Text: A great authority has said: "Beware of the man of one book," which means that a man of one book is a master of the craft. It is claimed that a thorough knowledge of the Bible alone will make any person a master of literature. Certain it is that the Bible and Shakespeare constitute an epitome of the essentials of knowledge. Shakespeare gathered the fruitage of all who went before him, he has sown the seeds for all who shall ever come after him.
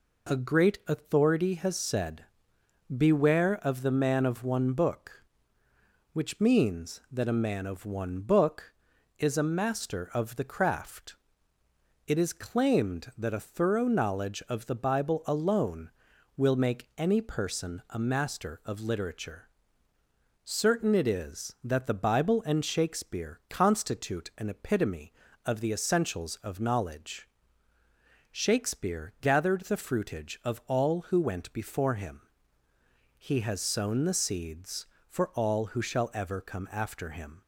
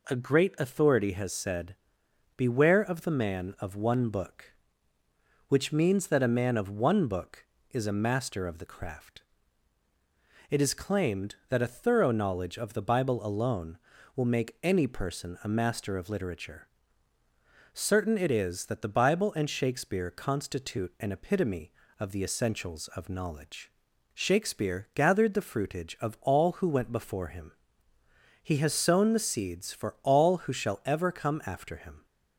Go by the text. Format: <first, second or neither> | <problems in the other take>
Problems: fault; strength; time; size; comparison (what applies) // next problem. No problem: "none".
neither | none